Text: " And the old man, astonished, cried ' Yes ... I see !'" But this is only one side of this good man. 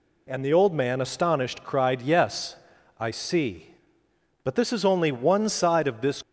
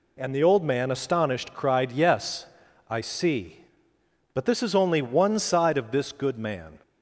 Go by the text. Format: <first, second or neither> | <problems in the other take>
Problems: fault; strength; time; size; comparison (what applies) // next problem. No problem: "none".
second | stops before "good man"; at 6.2 s